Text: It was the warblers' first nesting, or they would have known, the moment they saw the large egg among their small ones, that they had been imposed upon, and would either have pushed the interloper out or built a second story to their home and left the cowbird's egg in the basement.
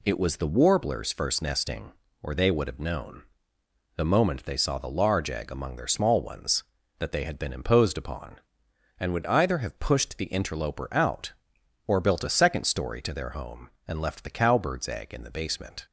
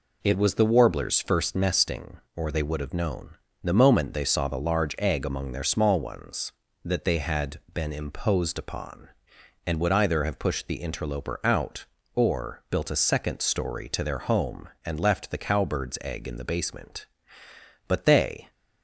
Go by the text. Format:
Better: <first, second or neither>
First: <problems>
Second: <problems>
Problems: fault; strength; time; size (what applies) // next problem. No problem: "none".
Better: first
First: none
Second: goes on to say "But they"; noticeable; from 17.8 s on; 0.62 s long